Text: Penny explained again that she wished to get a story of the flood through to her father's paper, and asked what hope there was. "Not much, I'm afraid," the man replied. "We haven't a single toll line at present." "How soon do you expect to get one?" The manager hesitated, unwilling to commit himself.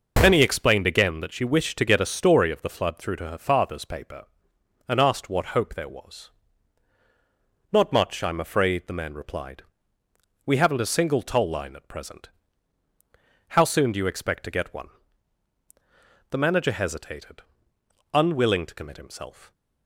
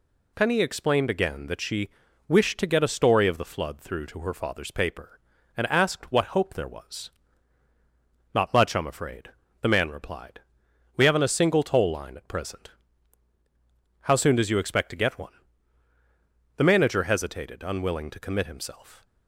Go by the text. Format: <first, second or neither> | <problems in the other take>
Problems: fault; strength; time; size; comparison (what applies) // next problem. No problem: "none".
first | pauses between "she" and "wished"; at 1.8 s; 0.38 s long // says "does" for "do"; at 14.3 s